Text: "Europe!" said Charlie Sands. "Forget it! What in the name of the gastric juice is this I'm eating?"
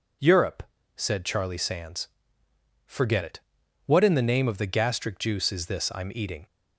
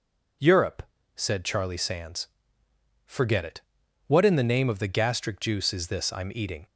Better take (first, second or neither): neither